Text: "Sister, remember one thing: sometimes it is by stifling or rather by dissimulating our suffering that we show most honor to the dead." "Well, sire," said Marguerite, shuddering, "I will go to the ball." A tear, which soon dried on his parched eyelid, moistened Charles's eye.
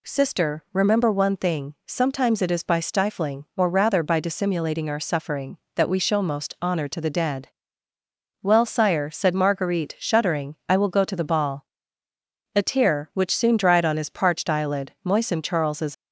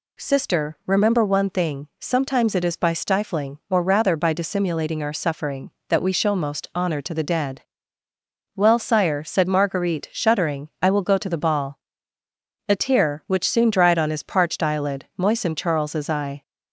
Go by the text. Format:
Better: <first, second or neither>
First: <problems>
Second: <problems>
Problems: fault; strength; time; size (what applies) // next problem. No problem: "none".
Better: second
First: stops before "eye"; at 15.9 s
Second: none